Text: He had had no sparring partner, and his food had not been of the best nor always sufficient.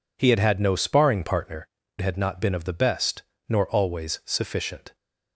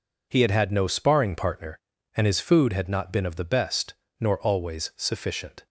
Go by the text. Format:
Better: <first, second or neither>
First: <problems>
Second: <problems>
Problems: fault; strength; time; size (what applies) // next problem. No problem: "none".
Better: second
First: skips "and his food"; at 1.8 s // pauses between "best" and "nor"; slight; at 3.2 s; 0.24 s long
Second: pauses between "best" and "nor"; slight; at 3.9 s; 0.24 s long